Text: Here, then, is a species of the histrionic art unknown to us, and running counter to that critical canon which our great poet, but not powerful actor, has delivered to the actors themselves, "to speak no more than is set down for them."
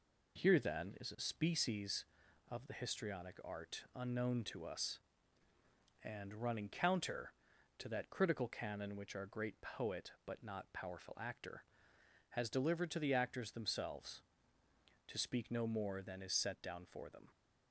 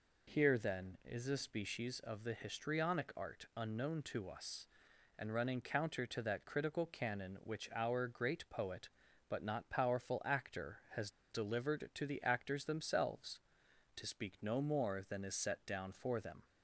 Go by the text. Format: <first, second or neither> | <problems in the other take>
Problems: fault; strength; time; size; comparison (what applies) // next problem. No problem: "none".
first | pauses between "has" and "delivered"; slight; at 11.0 s; 0.22 s long